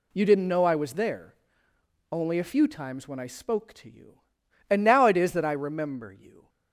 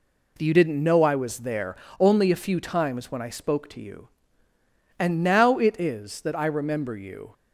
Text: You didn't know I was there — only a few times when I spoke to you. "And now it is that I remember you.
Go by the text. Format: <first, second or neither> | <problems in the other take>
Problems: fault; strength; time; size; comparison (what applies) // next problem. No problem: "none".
neither | none